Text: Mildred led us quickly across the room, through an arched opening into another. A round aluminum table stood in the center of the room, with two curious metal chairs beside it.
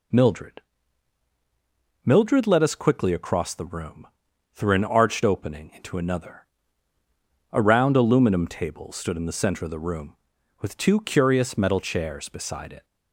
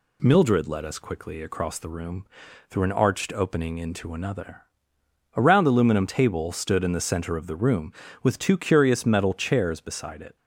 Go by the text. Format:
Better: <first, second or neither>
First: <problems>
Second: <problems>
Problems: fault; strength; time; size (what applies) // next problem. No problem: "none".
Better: second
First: says "Mildred" twice; at 2.0 s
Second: none